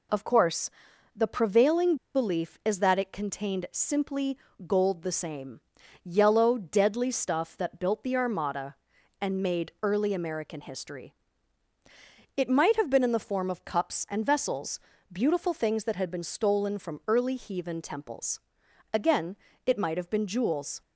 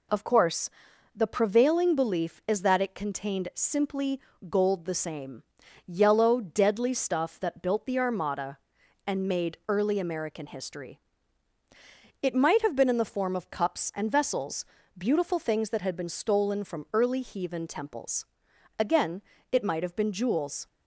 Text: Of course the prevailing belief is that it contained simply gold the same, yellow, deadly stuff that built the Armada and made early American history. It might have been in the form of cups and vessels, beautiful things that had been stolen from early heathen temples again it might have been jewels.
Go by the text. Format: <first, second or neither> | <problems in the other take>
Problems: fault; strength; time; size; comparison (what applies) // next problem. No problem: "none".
second | pauses between "course" and "the"; noticeable; at 0.7 s; 0.46 s long; noticeable in the second // pauses between "prevailing" and "belief"; slight; at 1.9 s; 0.18 s long // pauses between "simply" and "gold"; slight; at 4.3 s; 0.28 s long; slight in the second // pauses between "temples" and "again"; noticeable; at 18.3 s; 0.54 s long; noticeable in the second // pauses between "again" and "it"; slight; at 19.3 s; 0.30 s long; slight in the second